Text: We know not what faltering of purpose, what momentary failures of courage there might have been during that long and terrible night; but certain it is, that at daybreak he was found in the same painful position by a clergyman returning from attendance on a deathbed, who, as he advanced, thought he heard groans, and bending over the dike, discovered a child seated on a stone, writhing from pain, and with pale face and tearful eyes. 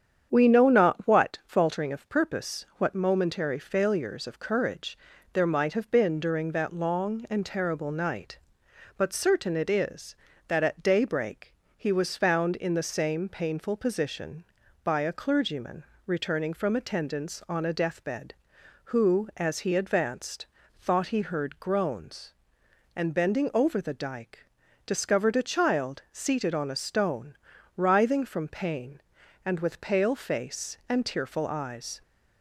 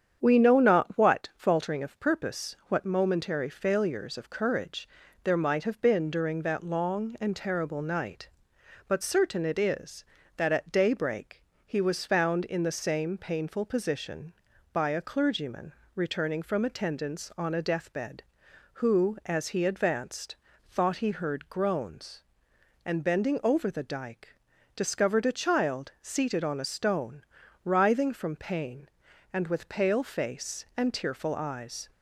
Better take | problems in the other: neither | starts louder than the rest; strong; the same in both // pauses between "courage" and "there"; slight; the same in both // pauses between "daybreak" and "he"; slight; the same in both // pauses between "clergyman" and "returning"; slight; the same in both

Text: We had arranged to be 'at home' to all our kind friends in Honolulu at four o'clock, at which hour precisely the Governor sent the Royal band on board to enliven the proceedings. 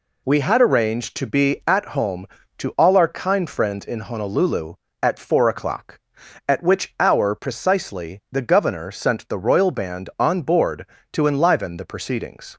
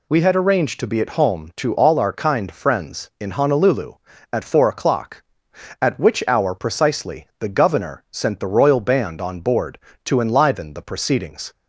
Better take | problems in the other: neither | none

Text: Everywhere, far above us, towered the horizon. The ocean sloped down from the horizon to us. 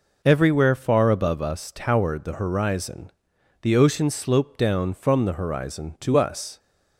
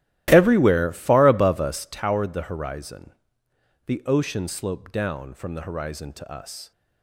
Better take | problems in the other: first | starts louder than the rest; strong; until 2.0 s; 14 dB

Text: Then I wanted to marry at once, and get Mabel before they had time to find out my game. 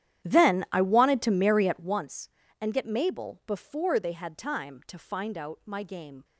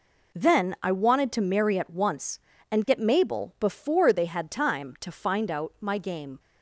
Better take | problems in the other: second | starts louder than the rest; strong; until 2.1 s; 11 dB

